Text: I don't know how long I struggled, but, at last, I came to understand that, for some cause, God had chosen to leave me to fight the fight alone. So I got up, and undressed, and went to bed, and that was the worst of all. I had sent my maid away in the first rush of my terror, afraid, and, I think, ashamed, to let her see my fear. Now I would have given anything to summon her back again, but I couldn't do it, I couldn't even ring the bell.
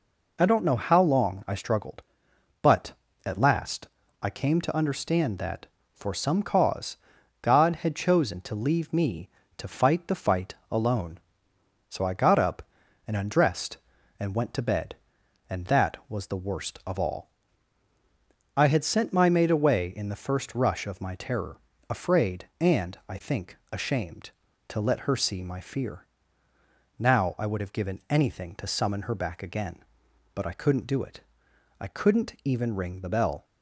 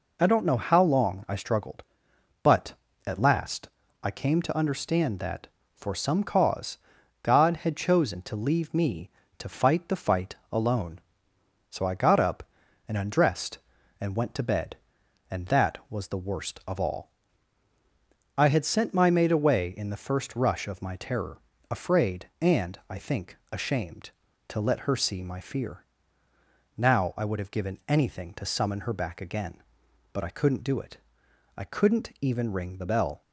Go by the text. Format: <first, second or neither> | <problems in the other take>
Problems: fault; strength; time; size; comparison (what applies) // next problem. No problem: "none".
neither | pauses between "fight" and "alone"; slight; the same in both